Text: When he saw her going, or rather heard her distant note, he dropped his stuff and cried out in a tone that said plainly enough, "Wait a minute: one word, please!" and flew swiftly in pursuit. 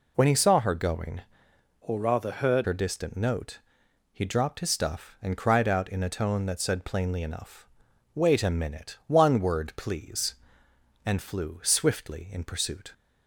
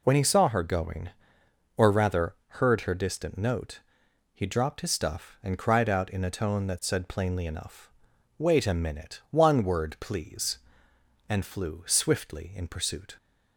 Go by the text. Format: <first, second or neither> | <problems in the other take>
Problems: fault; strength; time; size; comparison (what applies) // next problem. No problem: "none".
second | changes voice from "or" to "heard"; from 1.8 to 2.6 s; 0.8 s long